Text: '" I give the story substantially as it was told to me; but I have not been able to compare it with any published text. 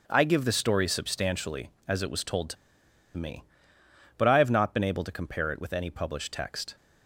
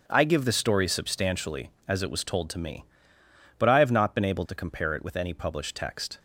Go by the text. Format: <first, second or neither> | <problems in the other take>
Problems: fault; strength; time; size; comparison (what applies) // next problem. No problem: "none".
second | starts louder than the rest; strong; until 1.0 s; 7.5 dB; also in the second // pauses between "to" and "me"; noticeable; at 2.5 s; 0.62 s long